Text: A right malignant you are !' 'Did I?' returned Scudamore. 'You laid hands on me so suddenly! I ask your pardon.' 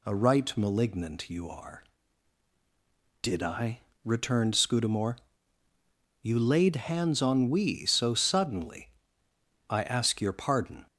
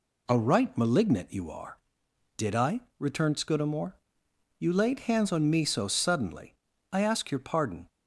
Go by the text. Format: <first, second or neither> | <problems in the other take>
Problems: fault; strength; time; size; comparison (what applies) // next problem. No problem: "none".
second | says "we" for "me"; at 7.4 s